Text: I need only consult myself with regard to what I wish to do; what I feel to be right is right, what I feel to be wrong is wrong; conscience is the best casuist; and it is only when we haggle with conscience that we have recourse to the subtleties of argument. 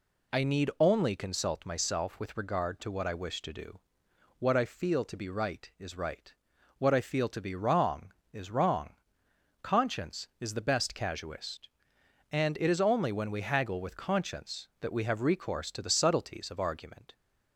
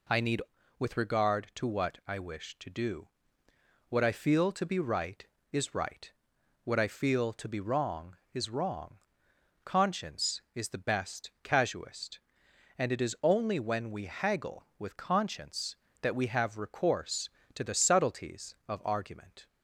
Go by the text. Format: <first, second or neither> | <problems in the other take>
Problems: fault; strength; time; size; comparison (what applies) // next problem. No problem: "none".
first | skips "only consult myself"; at 0.5 s